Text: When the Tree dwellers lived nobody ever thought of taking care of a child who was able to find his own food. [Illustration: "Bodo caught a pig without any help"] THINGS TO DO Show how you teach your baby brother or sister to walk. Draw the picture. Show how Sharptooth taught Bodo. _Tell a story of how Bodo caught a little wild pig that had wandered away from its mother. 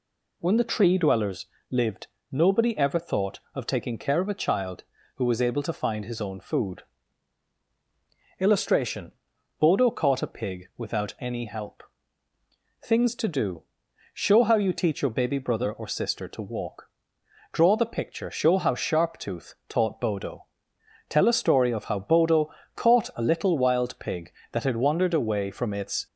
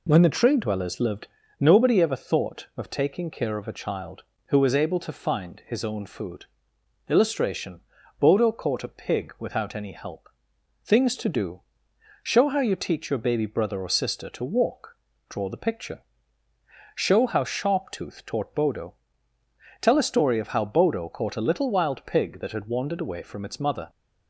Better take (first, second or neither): second